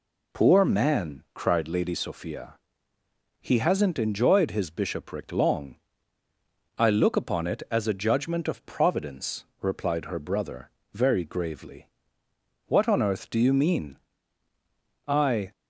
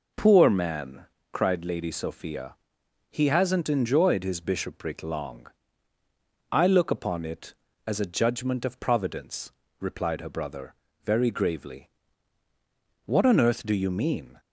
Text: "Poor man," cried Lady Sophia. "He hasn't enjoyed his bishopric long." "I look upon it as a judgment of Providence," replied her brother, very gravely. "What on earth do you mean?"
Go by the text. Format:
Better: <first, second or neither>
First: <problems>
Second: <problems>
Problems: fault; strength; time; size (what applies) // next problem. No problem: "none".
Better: second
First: goes on to say "I"; slight; from 15.0 s on; 0.44 s long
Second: none